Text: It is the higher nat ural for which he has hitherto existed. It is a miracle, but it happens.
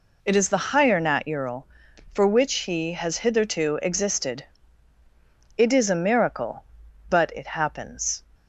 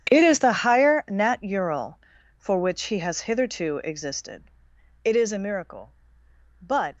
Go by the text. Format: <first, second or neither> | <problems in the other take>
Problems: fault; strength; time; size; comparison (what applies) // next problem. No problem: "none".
first | starts louder than the rest; strong; until 1.1 s; 9 dB // stops before "it happens"; at 6.9 s